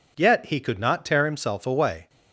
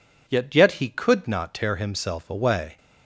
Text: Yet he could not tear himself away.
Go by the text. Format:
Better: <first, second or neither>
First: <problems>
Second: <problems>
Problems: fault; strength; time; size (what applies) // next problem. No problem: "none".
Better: first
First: none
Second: says "Yet" twice; at 0.5 s